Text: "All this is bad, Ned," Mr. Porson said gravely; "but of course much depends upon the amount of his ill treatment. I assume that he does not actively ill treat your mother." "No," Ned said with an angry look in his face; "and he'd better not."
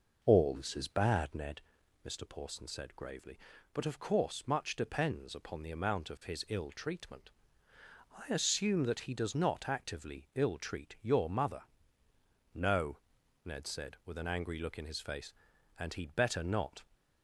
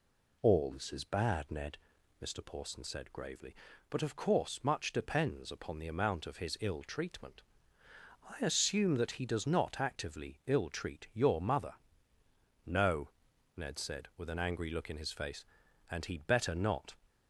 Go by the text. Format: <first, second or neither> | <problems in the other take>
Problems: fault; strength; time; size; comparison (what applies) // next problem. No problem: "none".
second | starts louder than the rest; noticeable; until 1.4 s; 5.5 dB